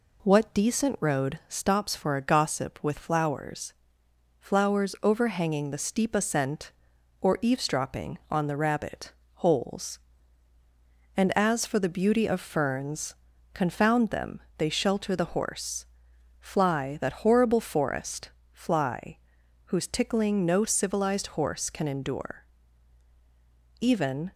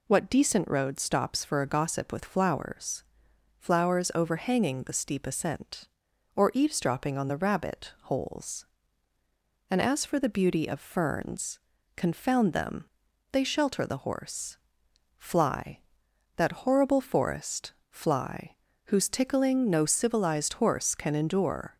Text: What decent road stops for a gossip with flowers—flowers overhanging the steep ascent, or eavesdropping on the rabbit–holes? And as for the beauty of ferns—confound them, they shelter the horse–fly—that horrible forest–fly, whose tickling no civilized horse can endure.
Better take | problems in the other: second | goes on to say "Even"; from 23.7 s on; 0.54 s long

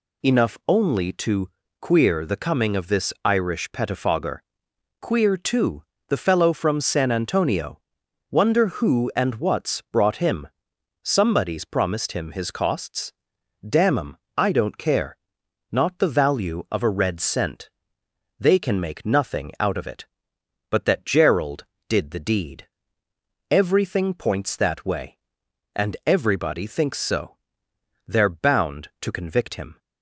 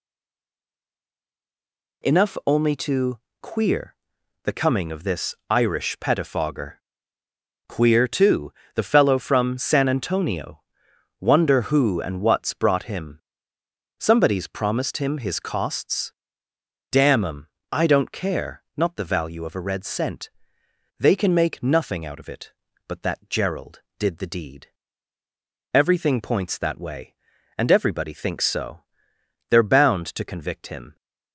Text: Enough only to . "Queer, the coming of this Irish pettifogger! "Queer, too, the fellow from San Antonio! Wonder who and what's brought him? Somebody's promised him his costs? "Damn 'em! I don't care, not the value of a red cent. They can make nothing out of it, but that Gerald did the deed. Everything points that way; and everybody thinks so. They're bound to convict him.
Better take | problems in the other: first | stays silent before the first word; noticeable; until 2.0 s; 2.0 s long // pauses between "this" and "Irish"; slight; at 5.3 s; 0.16 s long

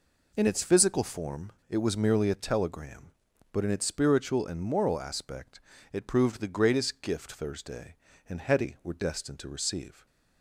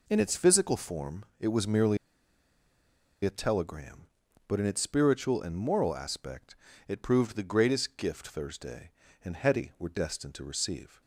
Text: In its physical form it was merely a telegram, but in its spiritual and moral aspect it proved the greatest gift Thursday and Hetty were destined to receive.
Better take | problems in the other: first | pauses between "form" and "it"; slight; at 1.2 s; 0.16 s long; slight in the first // pauses between "merely" and "a"; strong; at 1.9 s; 1.2 s long // pauses between "aspect" and "it"; slight; at 6.5 s; 0.32 s long; slight in the first

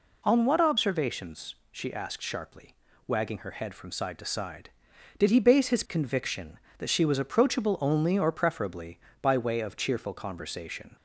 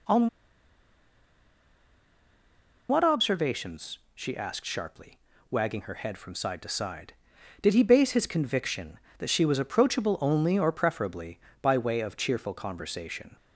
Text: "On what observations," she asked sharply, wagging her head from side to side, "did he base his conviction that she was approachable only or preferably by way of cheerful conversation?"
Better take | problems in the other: first | pauses between "On" and "what"; strong; at 0.2 s; 2.6 s long

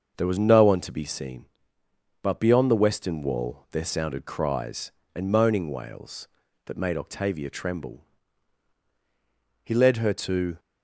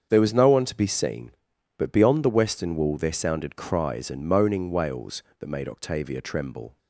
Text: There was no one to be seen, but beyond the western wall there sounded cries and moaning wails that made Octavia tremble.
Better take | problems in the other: second | starts louder than the rest; until 1.1 s; 6.5 dB; strong in the second // goes on to say "He led her to"; noticeable; from 9.6 s on; 0.94 s long

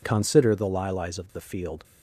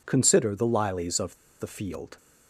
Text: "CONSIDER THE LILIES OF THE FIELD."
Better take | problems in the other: first | pauses between "OF" and "THE"; slight; at 1.3 s; 0.24 s long

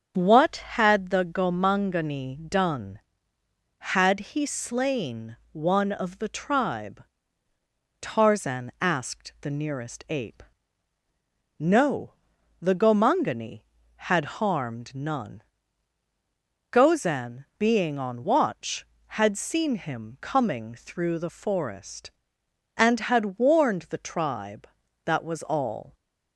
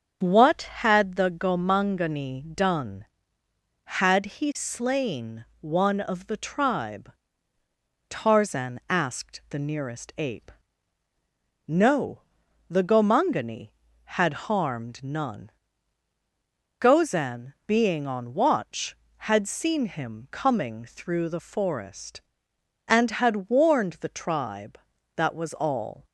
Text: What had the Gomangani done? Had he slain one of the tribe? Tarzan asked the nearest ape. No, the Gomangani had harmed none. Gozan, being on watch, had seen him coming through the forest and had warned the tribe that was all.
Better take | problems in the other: neither | starts louder than the rest; the same in both // pauses between "slain" and "one"; slight; the same in both // pauses between "had" and "harmed"; slight; the same in both

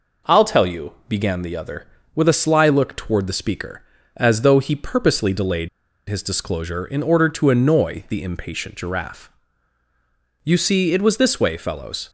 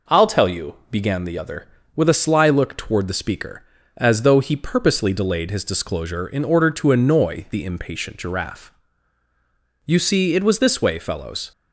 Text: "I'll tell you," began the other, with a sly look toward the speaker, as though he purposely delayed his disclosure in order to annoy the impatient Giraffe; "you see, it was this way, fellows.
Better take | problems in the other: second | pauses between "delayed" and "his"; at 5.6 s; 0.40 s long

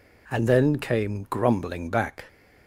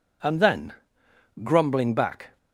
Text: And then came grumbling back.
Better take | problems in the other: first | skips "came"; at 1.0 s

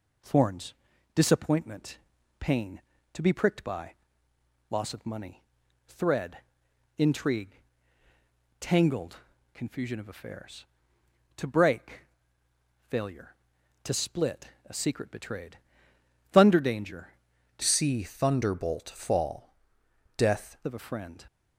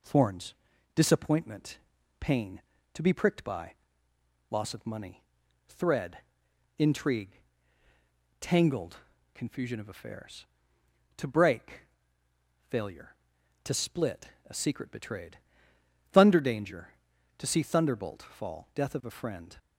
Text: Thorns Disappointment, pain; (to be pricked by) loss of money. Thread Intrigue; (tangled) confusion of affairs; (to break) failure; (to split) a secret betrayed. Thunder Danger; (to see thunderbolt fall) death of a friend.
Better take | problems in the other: second | pauses between "Thorns" and "Disappointment"; at 0.7 s; 0.42 s long; also in the second // pauses between "Thread" and "Intrigue"; noticeable; at 6.3 s; 0.58 s long; noticeable in the second // changes voice from "see" to "death"; from 17.6 to 20.5 s; 2.9 s long

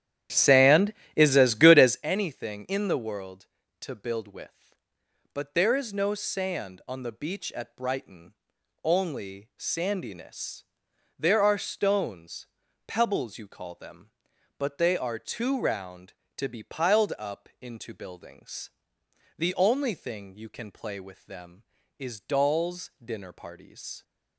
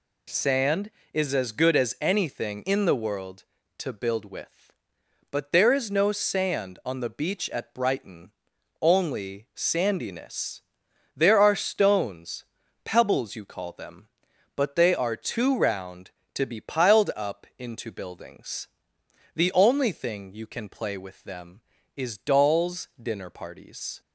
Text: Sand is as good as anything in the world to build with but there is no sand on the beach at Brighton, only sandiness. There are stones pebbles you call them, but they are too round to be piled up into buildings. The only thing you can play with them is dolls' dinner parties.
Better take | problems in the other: second | starts louder than the rest; strong; until 2.1 s; 11 dB // pauses between "stones" and "pebbles"; at 12.4 s; 0.38 s long; also in the second

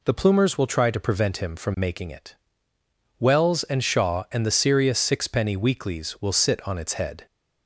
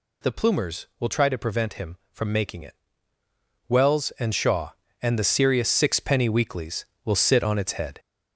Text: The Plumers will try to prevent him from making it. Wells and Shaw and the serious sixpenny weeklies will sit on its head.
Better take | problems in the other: first | gets louder; noticeable; throughout; 5 dB

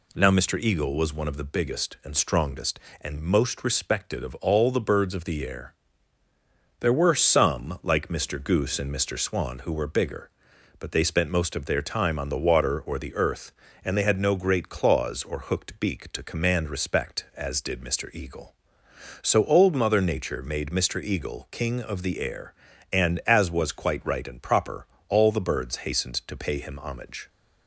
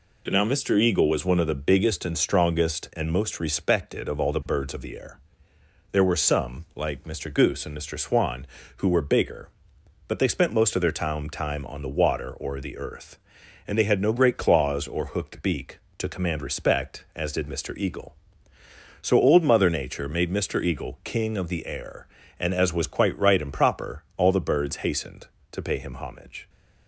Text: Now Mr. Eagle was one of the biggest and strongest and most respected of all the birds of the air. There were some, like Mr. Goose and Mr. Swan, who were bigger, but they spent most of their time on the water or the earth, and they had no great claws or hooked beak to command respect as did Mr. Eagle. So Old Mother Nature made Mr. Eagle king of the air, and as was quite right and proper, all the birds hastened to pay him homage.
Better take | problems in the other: first | says "time" twice; at 11.3 s

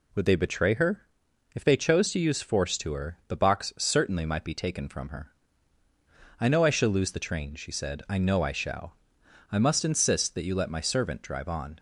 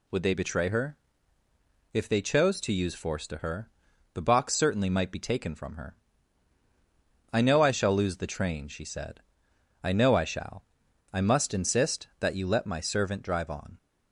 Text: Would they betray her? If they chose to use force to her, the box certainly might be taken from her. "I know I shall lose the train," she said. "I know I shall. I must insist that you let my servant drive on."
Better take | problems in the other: neither | none

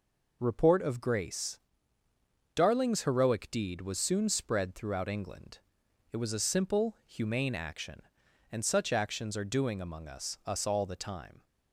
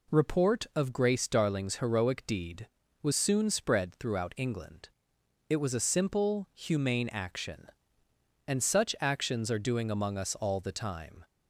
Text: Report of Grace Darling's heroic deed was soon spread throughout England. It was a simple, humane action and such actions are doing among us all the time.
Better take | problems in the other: second | pauses between "Grace" and "Darling's"; noticeable; at 1.6 s; 0.94 s long // says "us" twice; at 10.4 s

